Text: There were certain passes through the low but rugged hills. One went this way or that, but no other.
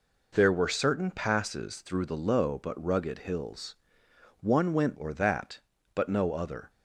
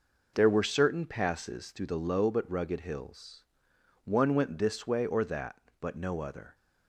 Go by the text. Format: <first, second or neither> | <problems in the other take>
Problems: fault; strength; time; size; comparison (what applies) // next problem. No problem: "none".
second | skips "this way"; at 4.9 s